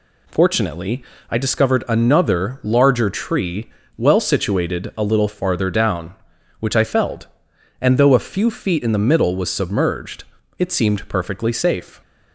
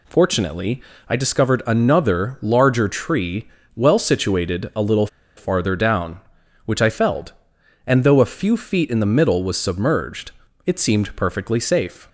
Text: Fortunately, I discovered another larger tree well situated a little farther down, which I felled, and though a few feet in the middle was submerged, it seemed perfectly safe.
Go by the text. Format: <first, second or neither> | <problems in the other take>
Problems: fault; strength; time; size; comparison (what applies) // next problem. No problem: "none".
first | pauses between "tree" and "well"; slight; at 3.4 s; 0.28 s long; slight in the first // pauses between "little" and "farther"; slight; at 5.0 s; 0.29 s long